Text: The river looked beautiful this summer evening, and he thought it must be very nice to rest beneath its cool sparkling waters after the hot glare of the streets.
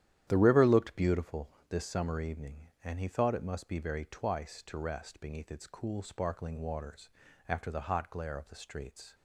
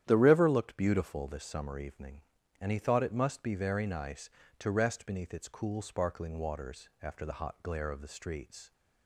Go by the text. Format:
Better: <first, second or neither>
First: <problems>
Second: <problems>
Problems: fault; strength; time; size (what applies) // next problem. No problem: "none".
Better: second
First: starts louder than the rest; strong; until 1.2 s; 11 dB // pauses between "beautiful" and "this"; slight; at 1.4 s; 0.22 s long // says "twice" for "nice"; at 4.0 s // pauses between "waters" and "after"; at 7.0 s; 0.40 s long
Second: starts louder than the rest; strong; until 1.0 s; 10.5 dB